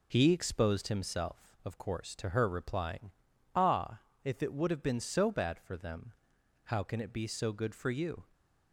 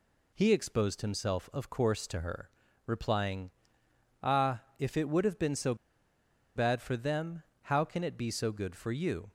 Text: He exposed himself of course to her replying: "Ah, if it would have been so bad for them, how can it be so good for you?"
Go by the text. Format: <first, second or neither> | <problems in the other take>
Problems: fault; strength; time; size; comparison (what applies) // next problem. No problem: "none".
first | pauses between "her" and "replying"; at 2.4 s; 0.38 s long // pauses between "so" and "bad"; noticeable; at 5.7 s; 0.80 s long